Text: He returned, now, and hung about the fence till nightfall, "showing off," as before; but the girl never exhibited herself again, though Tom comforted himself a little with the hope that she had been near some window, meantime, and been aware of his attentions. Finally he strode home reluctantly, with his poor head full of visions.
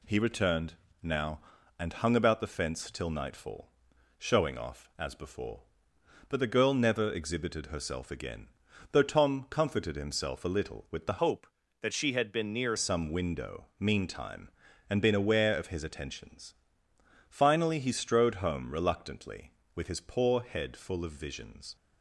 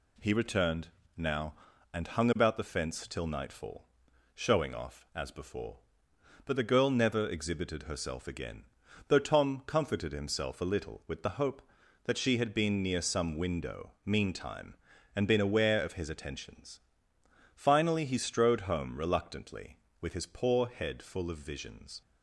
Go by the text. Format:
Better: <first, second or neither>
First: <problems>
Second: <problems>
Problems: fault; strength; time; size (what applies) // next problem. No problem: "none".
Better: second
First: changes voice from "hope" to "near"; from 11.1 to 12.7 s; 1.6 s long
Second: none